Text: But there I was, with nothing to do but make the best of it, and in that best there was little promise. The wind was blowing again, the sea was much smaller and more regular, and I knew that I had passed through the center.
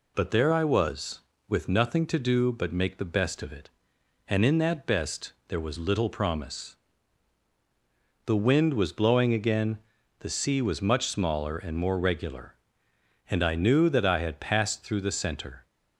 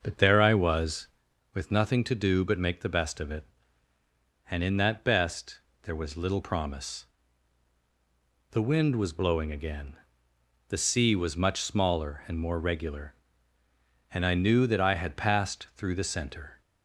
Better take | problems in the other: first | starts louder than the rest; noticeable; until 1.2 s; 6 dB // pauses between "best" and "there"; slight; at 5.6 s; 0.22 s long; slight in the first

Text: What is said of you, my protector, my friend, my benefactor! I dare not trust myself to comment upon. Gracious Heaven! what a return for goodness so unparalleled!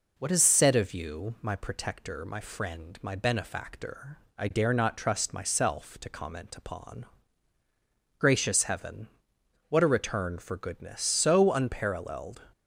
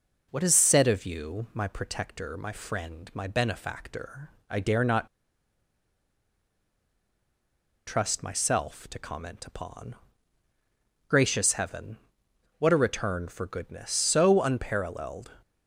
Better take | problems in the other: first | pauses between "not" and "trust"; strong; at 5.0 s; 2.7 s long

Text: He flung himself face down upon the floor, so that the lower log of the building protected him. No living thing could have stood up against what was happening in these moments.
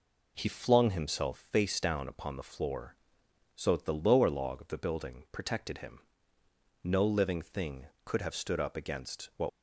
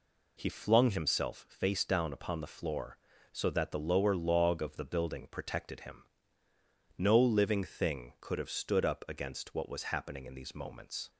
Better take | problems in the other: second | stops before "was happening in these moments"; at 9.4 s

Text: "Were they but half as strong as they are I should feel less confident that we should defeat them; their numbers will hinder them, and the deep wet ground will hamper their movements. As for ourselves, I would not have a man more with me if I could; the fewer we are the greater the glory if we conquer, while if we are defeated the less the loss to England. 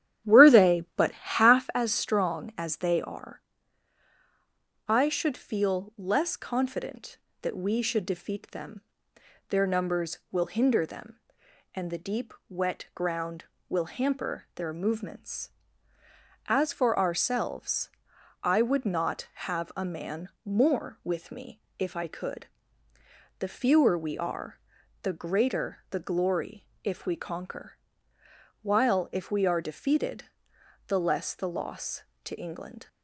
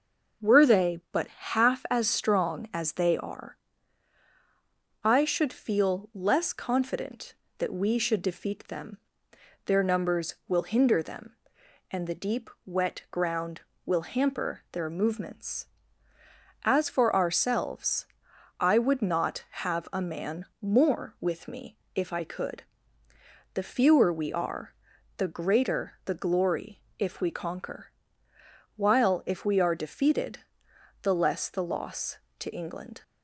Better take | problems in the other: second | starts louder than the rest; strong; until 1.8 s; 10.5 dB // pauses between "are" and "I"; strong; at 3.4 s; 1.4 s long; strong in the second // pauses between "deep" and "wet"; slight; at 12.3 s; 0.16 s long; slight in the second // pauses between "man" and "more"; slight; at 20.2 s; 0.16 s long; slight in the second // pauses between "me" and "if"; slight; at 21.6 s; 0.18 s long; slight in the second // pauses between "are" and "the"; at 24.5 s; 0.44 s long; also in the second // pauses between "glory" and "if"; slight; at 26.6 s; 0.16 s long; slight in the second // pauses between "defeated" and "the"; noticeable; at 30.2 s; 0.60 s long; noticeable in the second

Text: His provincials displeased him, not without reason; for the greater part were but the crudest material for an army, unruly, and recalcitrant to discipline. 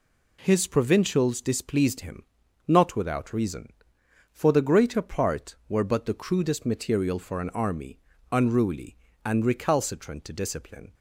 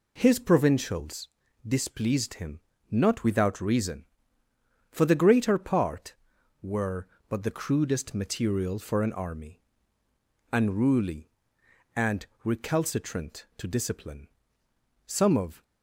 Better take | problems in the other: first | pauses between "provincials" and "displeased"; at 1.2 s; 0.40 s long // pauses between "and" and "recalcitrant"; slight; at 12.2 s; 0.20 s long // goes on to say "Some of"; from 15.0 s on; 0.58 s long

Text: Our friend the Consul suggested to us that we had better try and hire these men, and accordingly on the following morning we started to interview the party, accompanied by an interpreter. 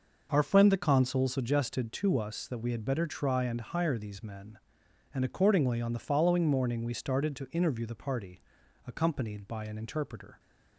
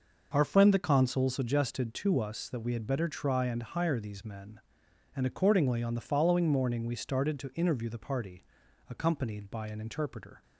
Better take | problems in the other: neither | none

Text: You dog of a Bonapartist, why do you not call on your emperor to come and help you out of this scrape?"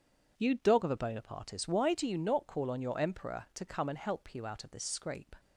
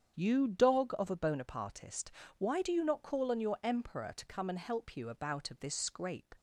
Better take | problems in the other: first | starts louder than the rest; strong; until 1.2 s; 8 dB // says "about" for "out"; at 5.0 s

